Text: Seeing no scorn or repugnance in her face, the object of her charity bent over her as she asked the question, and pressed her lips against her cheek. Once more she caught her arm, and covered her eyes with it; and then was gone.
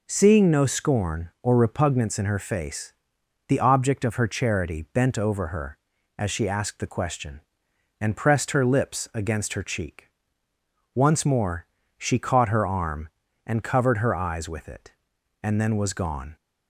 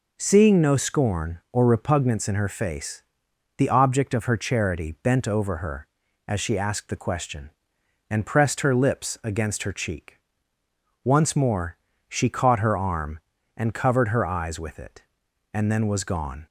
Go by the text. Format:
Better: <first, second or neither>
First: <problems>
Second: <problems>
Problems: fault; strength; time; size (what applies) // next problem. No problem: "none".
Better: neither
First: pauses between "more" and "she"; slight; at 11.6 s; 0.32 s long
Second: pauses between "more" and "she"; slight; at 11.7 s; 0.32 s long